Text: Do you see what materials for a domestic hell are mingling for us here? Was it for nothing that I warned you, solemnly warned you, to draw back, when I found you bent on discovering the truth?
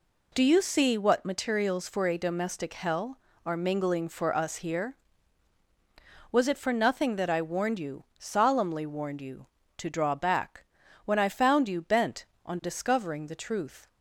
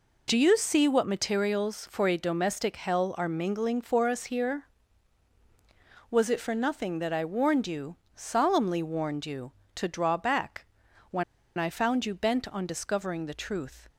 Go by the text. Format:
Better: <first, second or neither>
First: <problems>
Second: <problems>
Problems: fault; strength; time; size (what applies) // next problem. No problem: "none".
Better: first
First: none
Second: pauses between "when" and "I"; slight; at 11.2 s; 0.33 s long